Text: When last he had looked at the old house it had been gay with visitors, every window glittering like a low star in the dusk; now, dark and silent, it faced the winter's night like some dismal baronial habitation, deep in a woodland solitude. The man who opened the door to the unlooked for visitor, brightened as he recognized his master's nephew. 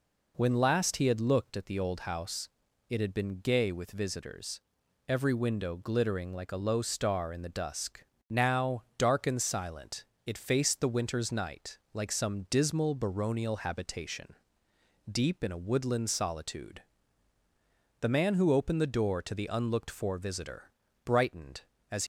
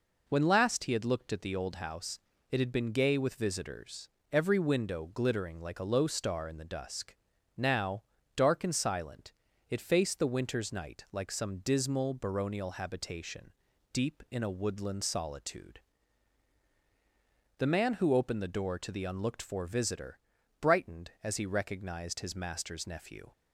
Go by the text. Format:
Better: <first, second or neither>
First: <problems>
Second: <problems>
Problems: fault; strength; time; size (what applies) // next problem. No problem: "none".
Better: second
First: pauses between "house" and "it"; at 2.4 s; 0.38 s long // stops before "he recognized his master's nephew"; at 22.0 s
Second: pauses between "house" and "it"; slight; at 2.1 s; 0.32 s long